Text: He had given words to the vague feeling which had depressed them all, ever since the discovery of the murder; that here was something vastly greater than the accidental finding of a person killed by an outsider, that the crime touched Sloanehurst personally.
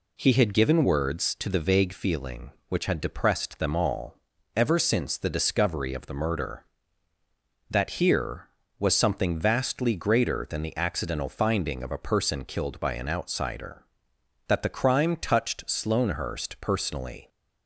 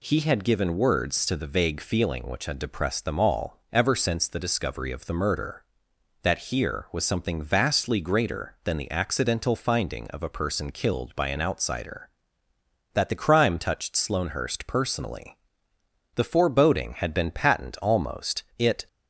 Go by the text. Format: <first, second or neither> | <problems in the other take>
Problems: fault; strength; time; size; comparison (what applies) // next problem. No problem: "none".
first | goes on to say "The foreboding had been patent almost it"; strong; from 16.1 s on; 2.7 s long